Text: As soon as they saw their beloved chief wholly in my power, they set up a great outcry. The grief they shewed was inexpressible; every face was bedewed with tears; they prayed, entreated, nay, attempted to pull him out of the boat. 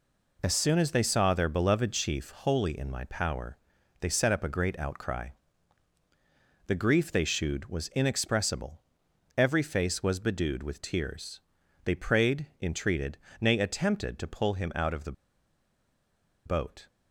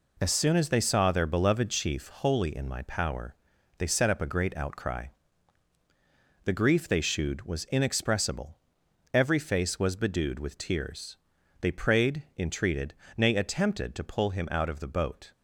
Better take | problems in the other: second | pauses between "the" and "boat"; strong; at 15.1 s; 1.3 s long

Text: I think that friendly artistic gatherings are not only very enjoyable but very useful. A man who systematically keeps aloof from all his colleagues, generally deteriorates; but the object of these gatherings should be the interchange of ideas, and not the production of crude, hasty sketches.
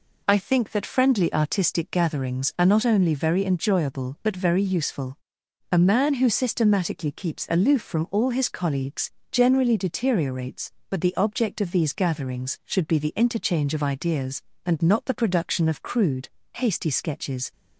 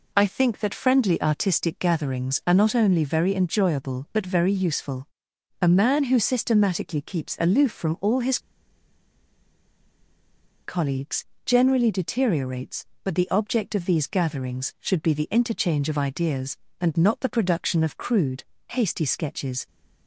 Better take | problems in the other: first | pauses between "his" and "colleagues"; strong; at 8.3 s; 2.2 s long

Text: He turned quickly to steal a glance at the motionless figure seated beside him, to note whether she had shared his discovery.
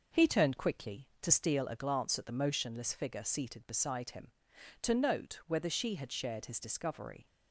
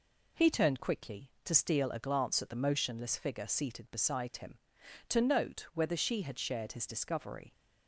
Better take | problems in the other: second | starts louder than the rest; noticeable; until 1.6 s; 5.5 dB

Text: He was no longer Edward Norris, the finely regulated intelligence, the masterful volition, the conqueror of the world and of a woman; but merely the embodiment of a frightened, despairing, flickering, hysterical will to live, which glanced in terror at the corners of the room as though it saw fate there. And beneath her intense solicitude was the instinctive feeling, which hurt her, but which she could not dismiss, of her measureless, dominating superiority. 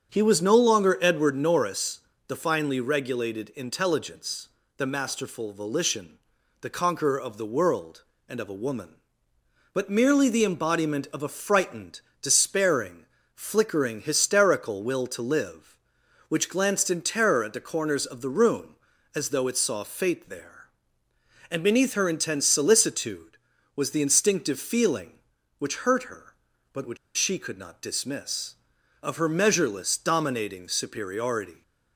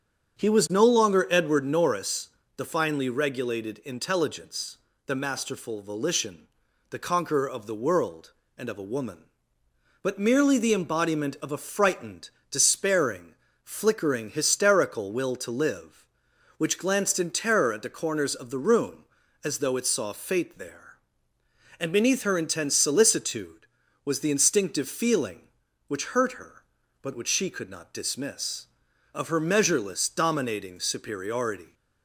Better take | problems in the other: second | starts louder than the rest; strong; until 1.1 s; 7.5 dB; strong in the second // pauses between "which" and "she"; slight; at 26.9 s; 0.20 s long

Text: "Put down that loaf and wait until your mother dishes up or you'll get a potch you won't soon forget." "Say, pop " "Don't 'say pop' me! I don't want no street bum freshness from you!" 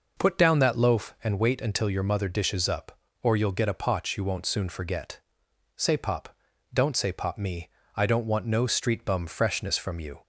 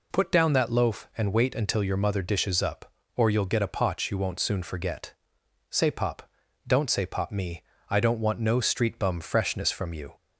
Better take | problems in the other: second | starts louder than the rest; noticeable; until 1.3 s; 5.5 dB

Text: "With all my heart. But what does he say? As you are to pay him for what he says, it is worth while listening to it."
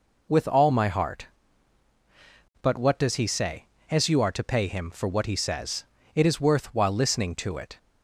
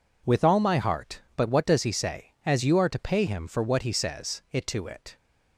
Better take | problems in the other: first | skips "is worth while listening"; at 4.6 s

